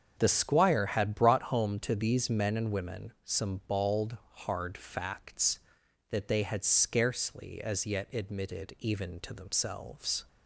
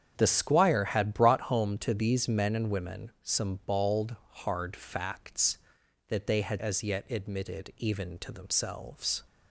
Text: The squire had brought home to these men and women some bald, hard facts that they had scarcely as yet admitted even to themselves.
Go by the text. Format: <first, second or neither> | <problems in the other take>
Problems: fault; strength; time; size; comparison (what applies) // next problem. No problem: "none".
first | starts louder than the rest; strong; until 1.1 s; 8 dB; also in the first // skips "scarcely"; at 6.5 s